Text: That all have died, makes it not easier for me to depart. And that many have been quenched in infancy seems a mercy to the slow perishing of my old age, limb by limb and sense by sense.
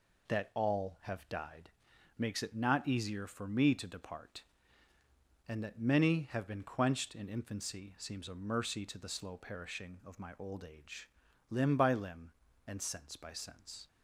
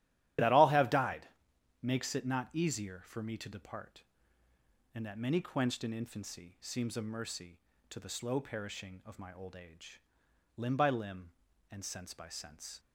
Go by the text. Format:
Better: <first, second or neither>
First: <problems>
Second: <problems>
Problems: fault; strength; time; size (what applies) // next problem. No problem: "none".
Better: first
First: none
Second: starts louder than the rest; strong; until 1.9 s; 12.5 dB // skips "have been"; at 5.4 s